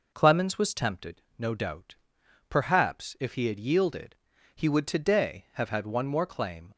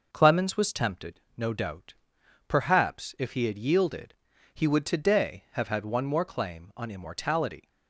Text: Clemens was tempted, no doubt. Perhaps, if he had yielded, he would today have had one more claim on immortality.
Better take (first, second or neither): second